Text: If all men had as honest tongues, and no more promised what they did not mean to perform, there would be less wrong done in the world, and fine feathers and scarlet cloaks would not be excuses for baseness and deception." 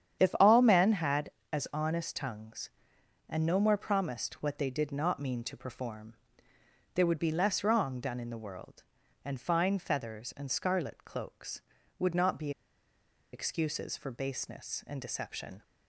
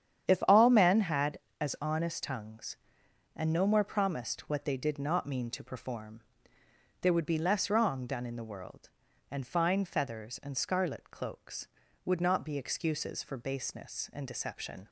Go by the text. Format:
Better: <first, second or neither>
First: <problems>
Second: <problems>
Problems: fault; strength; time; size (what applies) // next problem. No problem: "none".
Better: second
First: starts louder than the rest; strong; until 1.2 s; 9 dB // pauses between "be" and "excuses"; noticeable; at 12.5 s; 0.83 s long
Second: starts louder than the rest; strong; until 1.3 s; 9 dB